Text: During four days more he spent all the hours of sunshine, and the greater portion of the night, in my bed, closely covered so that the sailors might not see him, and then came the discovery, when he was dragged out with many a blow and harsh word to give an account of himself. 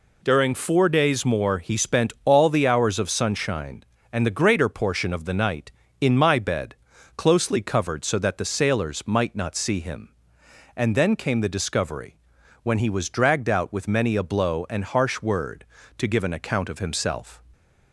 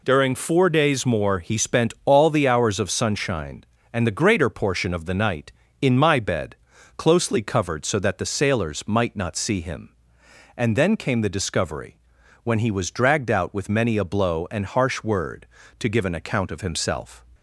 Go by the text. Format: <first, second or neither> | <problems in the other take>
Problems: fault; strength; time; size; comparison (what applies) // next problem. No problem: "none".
neither | none